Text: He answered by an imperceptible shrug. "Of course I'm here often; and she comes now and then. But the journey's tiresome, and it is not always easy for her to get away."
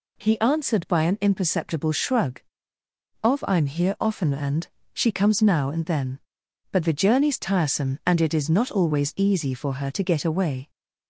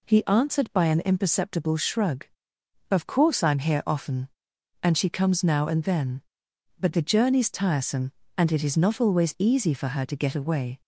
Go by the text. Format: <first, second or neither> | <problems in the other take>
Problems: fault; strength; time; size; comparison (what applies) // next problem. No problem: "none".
second | skips "course"; at 3.4 s // pauses between "and" and "she"; slight; at 4.6 s; 0.28 s long